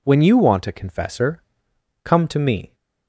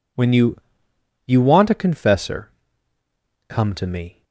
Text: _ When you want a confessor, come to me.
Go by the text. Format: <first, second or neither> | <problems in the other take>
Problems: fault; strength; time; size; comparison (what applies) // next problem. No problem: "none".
first | says "you" twice; at 1.2 s